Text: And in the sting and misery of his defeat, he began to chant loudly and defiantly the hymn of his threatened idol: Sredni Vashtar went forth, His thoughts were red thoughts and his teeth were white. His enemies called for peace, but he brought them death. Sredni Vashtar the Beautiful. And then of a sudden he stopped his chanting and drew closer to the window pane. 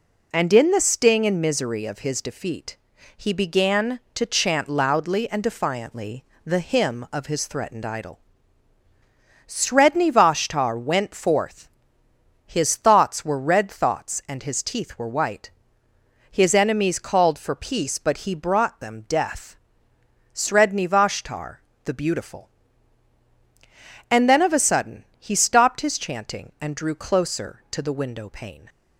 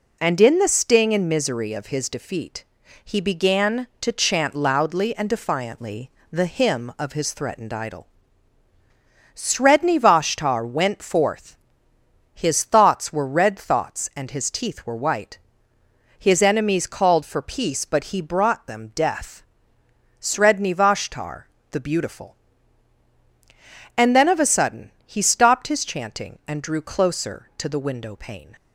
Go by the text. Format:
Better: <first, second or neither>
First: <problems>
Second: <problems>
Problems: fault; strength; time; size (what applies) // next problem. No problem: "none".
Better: neither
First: pauses between "defiantly" and "the"; slight; at 6.2 s; 0.20 s long // pauses between "Vashtar" and "the"; slight; at 21.5 s; 0.28 s long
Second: pauses between "defiantly" and "the"; slight; at 6.1 s; 0.20 s long // pauses between "Vashtar" and "the"; slight; at 21.4 s; 0.28 s long